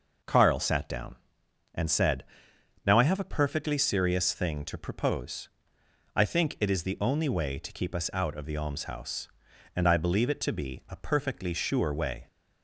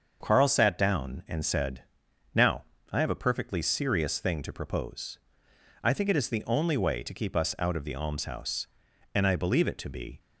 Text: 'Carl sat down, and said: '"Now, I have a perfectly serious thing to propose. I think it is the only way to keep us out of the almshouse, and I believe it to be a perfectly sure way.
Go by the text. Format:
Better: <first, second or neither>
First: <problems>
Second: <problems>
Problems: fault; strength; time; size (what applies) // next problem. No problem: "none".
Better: first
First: none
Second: starts louder than the rest; until 1.2 s; 6.5 dB // stops before "a perfectly sure way"; at 10.1 s